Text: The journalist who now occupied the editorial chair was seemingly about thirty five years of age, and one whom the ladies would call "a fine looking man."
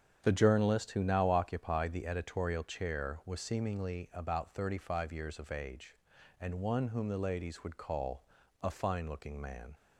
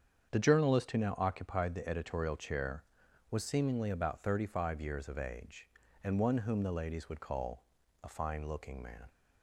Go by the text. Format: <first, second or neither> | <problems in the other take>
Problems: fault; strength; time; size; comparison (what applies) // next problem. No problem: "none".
neither | starts louder than the rest; strong; the same in both // pauses between "call" and "a"; the same in both